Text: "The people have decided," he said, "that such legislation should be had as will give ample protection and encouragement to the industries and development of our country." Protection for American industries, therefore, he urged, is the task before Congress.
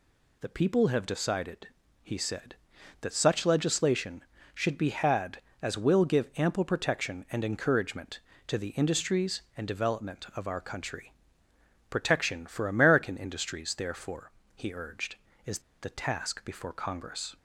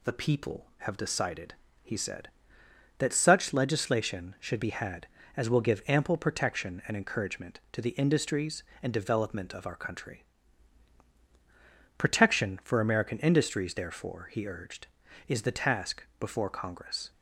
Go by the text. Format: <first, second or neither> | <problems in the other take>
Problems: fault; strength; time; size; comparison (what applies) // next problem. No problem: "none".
second | pauses between "is" and "the"; slight; at 15.6 s; 0.22 s long